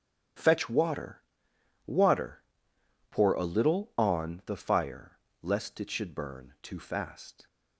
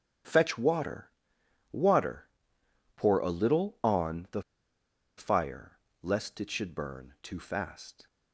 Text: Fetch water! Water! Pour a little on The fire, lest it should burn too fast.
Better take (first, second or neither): first